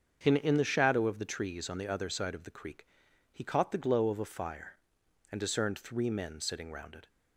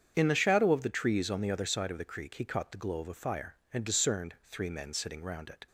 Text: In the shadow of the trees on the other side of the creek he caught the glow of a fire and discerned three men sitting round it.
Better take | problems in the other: second | starts louder than the rest; strong; until 1.2 s; 7 dB; strong in the second // says "In" twice; at 0.3 s // pauses between "creek" and "he"; noticeable; at 2.8 s; 0.46 s long

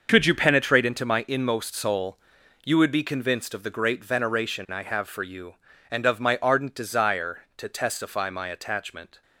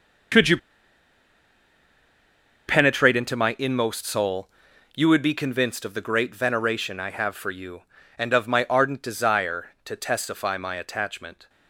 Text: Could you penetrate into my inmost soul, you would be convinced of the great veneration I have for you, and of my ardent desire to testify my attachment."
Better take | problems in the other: first | starts louder than the rest; until 3.4 s; 6.5 dB; also in the first // pauses between "you" and "penetrate"; strong; at 0.5 s; 2.1 s long

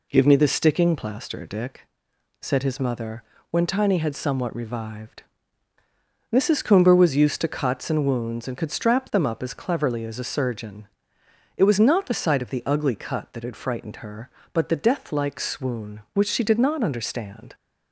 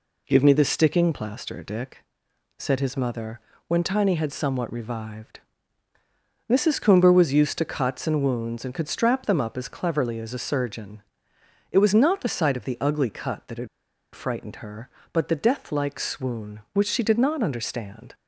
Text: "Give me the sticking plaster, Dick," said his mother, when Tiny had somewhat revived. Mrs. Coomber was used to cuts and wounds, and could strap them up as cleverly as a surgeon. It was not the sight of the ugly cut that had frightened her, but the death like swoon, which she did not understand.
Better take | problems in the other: first | pauses between "had" and "frightened"; noticeable; at 13.6 s; 0.46 s long

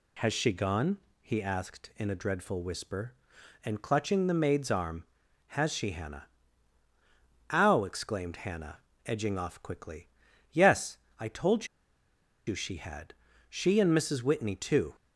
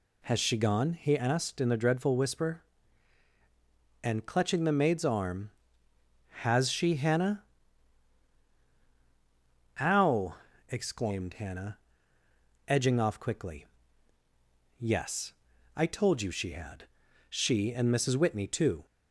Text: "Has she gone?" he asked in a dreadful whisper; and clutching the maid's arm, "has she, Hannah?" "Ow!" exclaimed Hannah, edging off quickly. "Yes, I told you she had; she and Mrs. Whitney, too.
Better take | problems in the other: second | pauses between "told" and "you"; noticeable; at 11.6 s; 0.79 s long

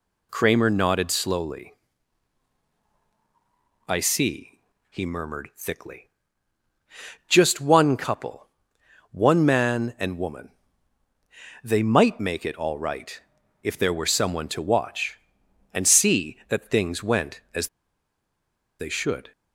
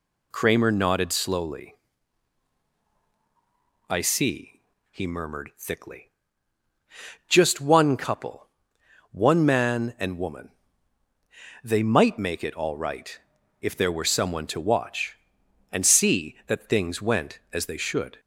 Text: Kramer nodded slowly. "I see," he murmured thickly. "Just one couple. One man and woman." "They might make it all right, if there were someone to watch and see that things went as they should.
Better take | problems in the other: second | pauses between "as" and "they"; at 17.6 s; 1.1 s long

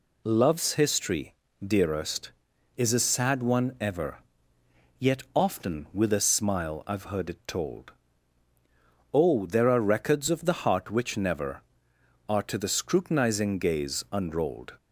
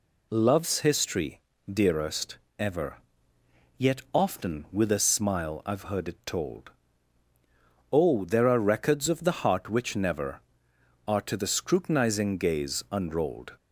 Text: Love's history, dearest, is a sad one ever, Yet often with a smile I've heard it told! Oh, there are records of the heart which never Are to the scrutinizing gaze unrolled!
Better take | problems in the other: first | skips "is a sad one"; at 2.4 s

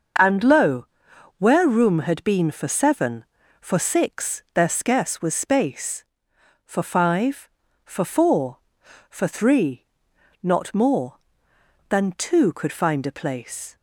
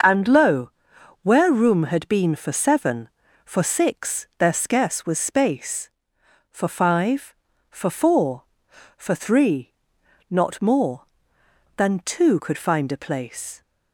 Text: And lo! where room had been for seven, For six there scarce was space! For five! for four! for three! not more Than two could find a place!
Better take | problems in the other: neither | starts louder than the rest; the same in both

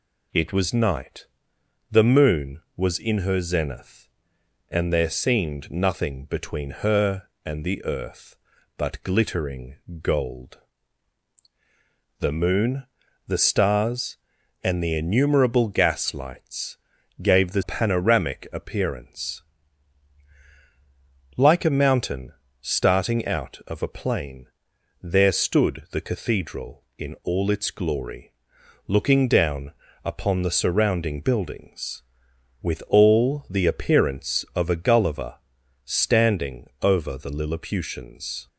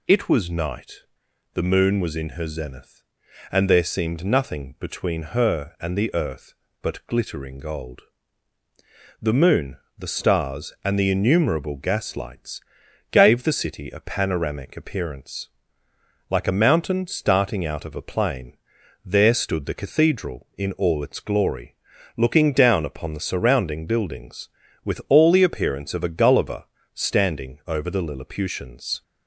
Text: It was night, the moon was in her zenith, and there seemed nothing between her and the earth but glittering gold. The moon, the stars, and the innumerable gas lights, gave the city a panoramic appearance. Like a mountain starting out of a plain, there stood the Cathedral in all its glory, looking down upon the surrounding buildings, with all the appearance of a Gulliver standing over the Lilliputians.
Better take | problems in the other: second | pauses between "glittering" and "gold"; slight; at 9.7 s; 0.24 s long // skips "city a"; at 17.6 s // pauses between "mountain" and "starting"; slight; at 22.3 s; 0.28 s long // pauses between "down" and "upon"; slight; at 29.7 s; 0.32 s long // pauses between "Gulliver" and "standing"; noticeable; at 35.3 s; 0.50 s long; slight in the second

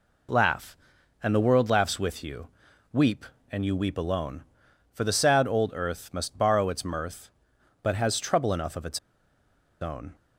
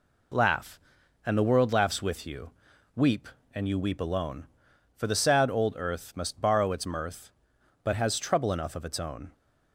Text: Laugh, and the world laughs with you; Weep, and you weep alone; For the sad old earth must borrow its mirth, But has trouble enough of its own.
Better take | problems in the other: second | pauses between "its" and "own"; noticeable; at 8.9 s; 0.82 s long

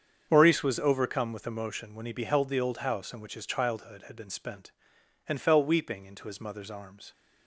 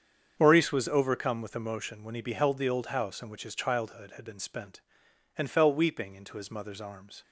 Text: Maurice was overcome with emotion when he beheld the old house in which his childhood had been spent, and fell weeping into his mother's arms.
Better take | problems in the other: neither | starts louder than the rest; strong; the same in both

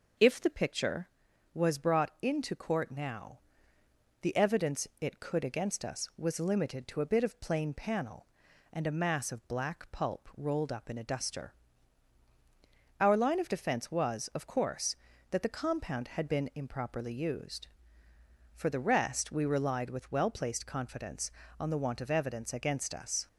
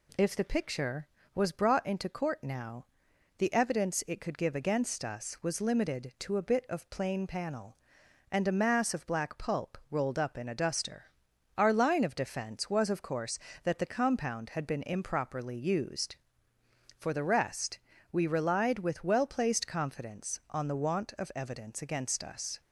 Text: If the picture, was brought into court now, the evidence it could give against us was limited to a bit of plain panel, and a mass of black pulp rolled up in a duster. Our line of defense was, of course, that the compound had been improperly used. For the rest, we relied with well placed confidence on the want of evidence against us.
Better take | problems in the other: second | skips "give"; at 5.4 s

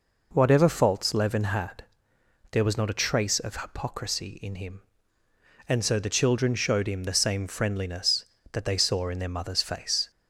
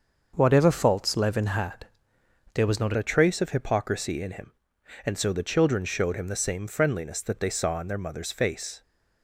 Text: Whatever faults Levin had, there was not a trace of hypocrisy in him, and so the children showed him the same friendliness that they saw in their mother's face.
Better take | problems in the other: first | starts louder than the rest; until 1.3 s; 6.5 dB // changes voice at "a"; from 2.9 s on; 5.9 s long

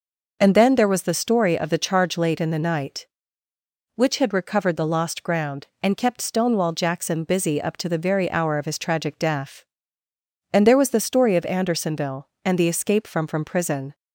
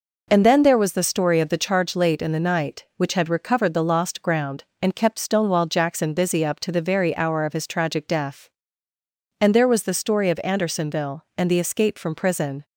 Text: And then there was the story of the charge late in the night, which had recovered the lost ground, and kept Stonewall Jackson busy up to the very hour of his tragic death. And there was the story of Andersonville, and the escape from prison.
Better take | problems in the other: second | says "from" twice; at 13.2 s

